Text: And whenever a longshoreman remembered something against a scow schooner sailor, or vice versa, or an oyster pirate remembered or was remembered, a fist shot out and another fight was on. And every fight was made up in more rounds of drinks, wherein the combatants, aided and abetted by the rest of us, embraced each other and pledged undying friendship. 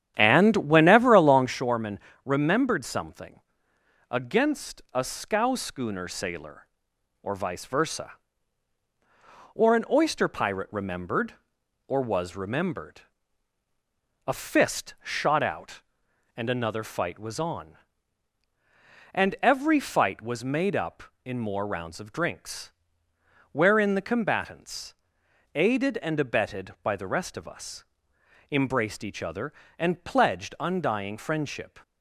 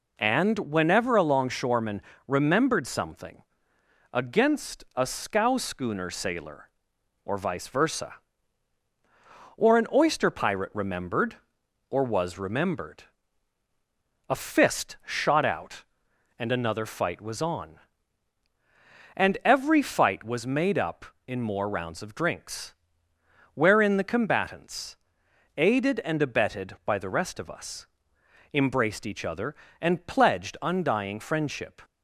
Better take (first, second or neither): second